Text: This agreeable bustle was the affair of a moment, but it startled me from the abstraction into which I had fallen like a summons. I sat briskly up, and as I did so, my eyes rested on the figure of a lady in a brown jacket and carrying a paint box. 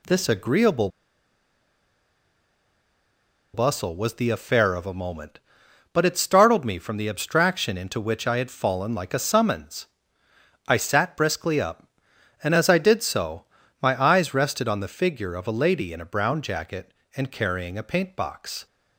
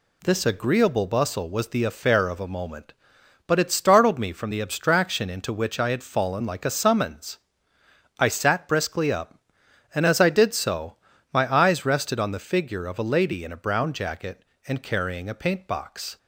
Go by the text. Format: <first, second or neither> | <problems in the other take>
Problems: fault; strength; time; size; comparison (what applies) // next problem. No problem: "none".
second | pauses between "agreeable" and "bustle"; strong; at 0.8 s; 2.6 s long